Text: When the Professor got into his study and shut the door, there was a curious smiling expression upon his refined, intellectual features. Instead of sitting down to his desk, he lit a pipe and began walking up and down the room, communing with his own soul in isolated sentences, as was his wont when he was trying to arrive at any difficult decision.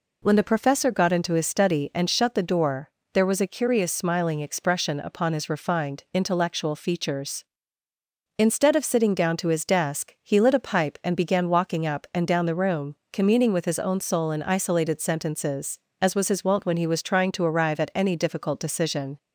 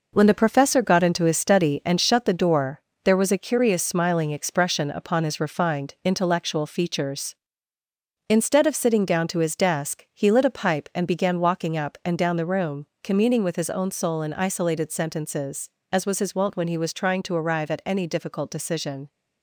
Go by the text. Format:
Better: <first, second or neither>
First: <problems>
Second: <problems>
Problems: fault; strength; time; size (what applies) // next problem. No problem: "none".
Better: first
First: none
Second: gets quieter; noticeable; throughout; 5.5 dB